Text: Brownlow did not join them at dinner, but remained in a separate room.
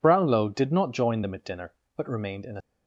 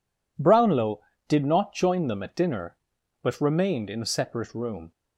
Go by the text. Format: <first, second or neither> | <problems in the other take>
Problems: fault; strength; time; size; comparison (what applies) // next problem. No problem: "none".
second | stops before "separate room"; at 2.6 s